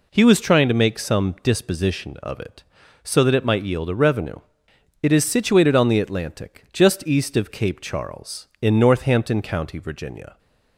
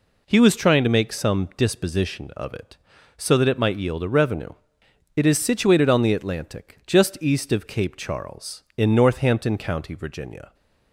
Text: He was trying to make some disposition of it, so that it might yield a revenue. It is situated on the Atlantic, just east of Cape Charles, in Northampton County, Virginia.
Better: neither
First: none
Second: none

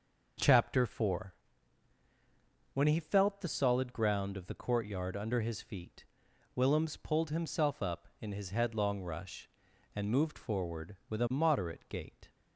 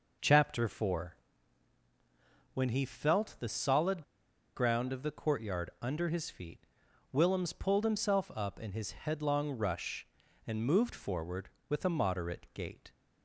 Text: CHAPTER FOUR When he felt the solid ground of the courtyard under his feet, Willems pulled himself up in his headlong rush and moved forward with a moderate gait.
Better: first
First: pauses between "FOUR" and "When"; strong; at 1.3 s; 1.4 s long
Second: pauses between "FOUR" and "When"; strong; at 1.1 s; 1.3 s long // pauses between "solid" and "ground"; noticeable; at 4.0 s; 0.52 s long

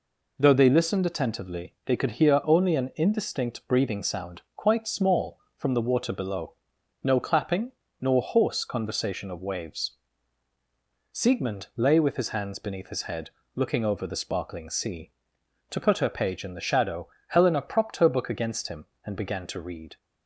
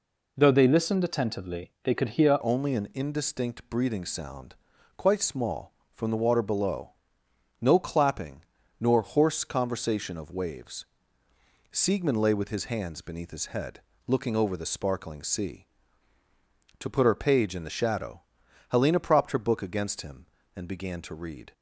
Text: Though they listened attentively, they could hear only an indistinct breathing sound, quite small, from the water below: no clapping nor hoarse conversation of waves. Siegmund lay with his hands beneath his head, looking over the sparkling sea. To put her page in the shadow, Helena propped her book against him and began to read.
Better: first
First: pauses between "clapping" and "nor"; slight; at 7.7 s; 0.30 s long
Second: changes voice at "only"; from 2.4 s on; 19.1 s long // pauses between "clapping" and "nor"; at 8.4 s; 0.38 s long

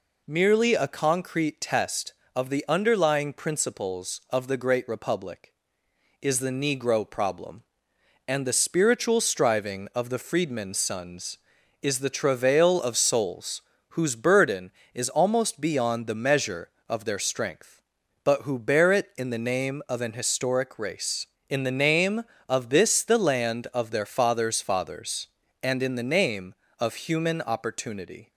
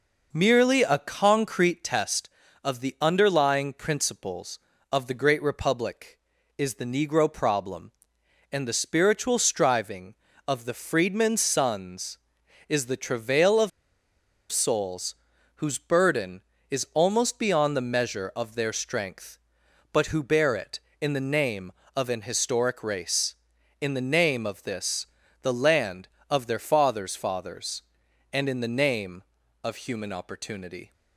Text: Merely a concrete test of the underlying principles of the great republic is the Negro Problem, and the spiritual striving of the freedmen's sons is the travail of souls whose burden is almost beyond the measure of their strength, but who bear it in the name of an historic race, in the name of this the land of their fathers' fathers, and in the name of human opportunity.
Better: first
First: pauses between "souls" and "whose"; slight; at 13.6 s; 0.32 s long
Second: pauses between "of" and "souls"; noticeable; at 13.7 s; 0.81 s long // pauses between "souls" and "whose"; at 15.1 s; 0.40 s long // pauses between "this" and "the"; slight; at 25.0 s; 0.34 s long

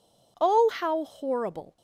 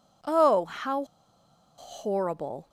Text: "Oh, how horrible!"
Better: first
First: none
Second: pauses between "how" and "horrible"; noticeable; at 1.0 s; 0.73 s long

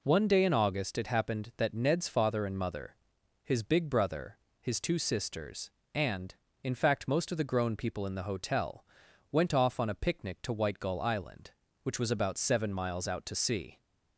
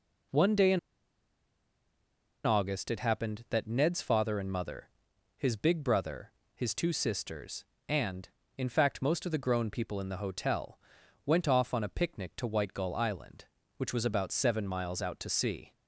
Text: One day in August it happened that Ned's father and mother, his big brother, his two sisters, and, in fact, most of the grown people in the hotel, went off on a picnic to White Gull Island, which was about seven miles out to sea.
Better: first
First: none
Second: pauses between "in" and "August"; strong; at 0.7 s; 1.6 s long

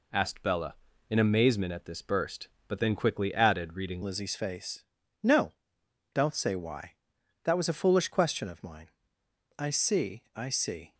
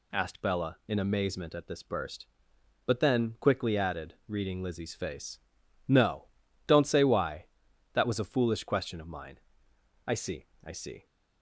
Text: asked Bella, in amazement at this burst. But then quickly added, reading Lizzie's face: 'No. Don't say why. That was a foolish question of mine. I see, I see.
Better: second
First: changes voice at "Lizzie's"; from 4.0 s on; 6.9 s long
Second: none

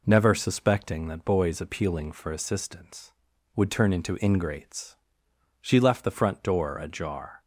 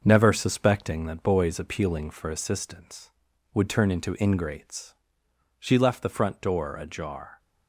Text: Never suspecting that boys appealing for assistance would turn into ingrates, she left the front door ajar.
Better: first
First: none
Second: gets quieter; noticeable; throughout; 5 dB

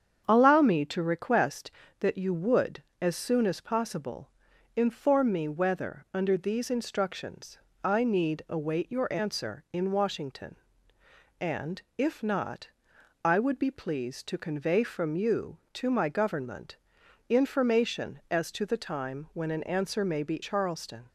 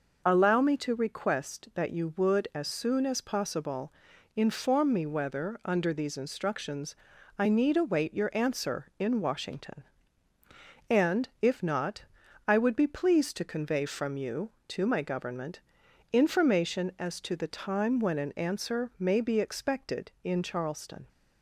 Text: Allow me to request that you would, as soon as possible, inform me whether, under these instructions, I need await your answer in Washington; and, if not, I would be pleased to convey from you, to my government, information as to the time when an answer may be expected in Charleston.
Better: second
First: starts louder than the rest; strong; until 1.2 s; 8 dB // skips "expected in"; at 20.4 s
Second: none

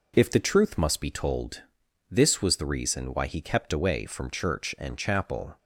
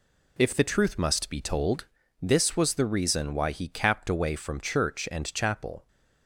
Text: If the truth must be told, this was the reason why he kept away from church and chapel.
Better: first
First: none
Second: says "capped" for "kept"; at 3.6 s

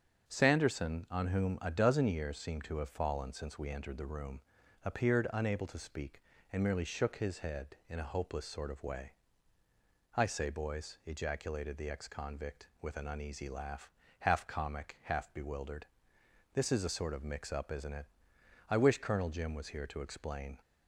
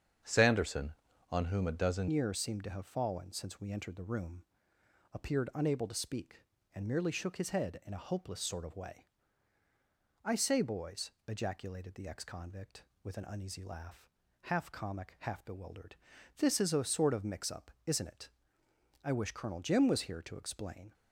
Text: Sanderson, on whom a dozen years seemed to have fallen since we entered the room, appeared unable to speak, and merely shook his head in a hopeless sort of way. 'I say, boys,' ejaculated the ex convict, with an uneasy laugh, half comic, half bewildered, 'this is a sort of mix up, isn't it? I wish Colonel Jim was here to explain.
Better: first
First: starts louder than the rest; until 1.3 s; 7 dB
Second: starts louder than the rest; strong; until 1.6 s; 8 dB // changes voice at "years"; from 2.0 s on; 18.9 s long

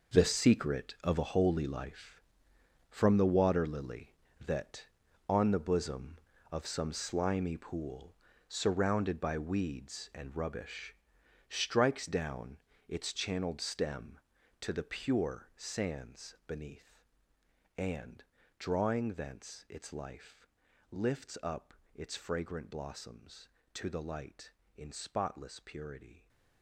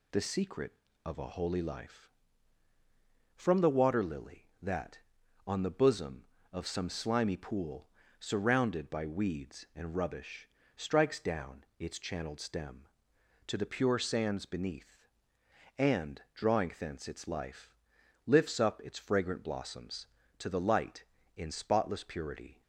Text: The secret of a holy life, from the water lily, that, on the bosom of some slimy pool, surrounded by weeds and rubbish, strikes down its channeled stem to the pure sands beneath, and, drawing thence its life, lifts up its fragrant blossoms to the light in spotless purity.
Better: second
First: gets quieter; strong; throughout; 12.5 dB // pauses between "down" and "its"; slight; at 12.5 s; 0.30 s long // pauses between "up" and "its"; slight; at 21.7 s; 0.22 s long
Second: none

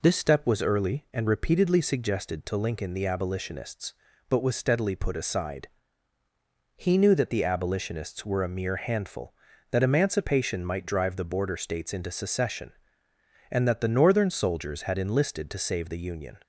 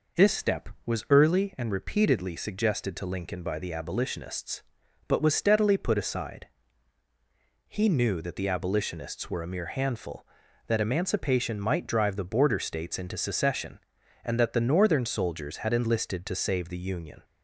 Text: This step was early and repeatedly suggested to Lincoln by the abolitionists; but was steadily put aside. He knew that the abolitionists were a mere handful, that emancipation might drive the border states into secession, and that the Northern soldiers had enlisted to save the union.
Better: second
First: skips "by"; at 2.9 s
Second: none

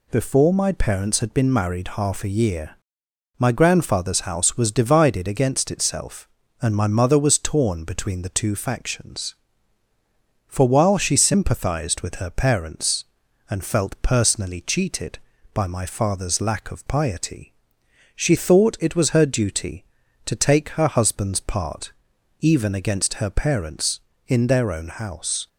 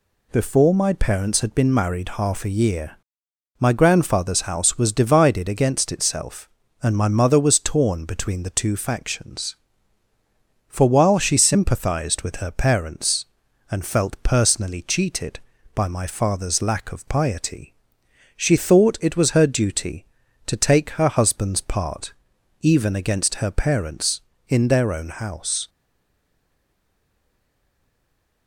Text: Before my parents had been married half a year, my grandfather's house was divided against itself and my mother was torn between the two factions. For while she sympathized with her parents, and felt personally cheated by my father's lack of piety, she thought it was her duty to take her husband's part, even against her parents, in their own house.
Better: first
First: none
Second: stays silent after the last word; strong; from 25.6 s on; 2.8 s long

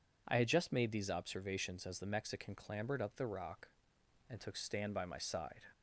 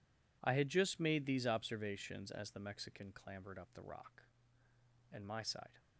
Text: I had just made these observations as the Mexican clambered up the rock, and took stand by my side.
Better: first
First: none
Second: skips "took stand by"; at 5.2 s

